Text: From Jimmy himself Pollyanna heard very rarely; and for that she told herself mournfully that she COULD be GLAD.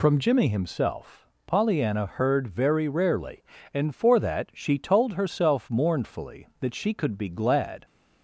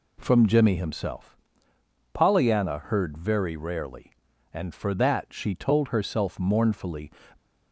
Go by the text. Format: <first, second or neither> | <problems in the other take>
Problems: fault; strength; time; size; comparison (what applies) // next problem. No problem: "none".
first | pauses between "himself" and "Pollyanna"; noticeable; at 1.3 s; 0.76 s long; slight in the first // stops before "that she COULD be GLAD"; at 7.3 s